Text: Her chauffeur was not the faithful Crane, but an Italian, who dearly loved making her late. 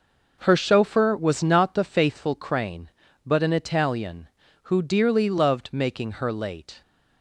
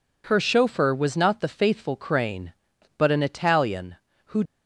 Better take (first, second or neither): first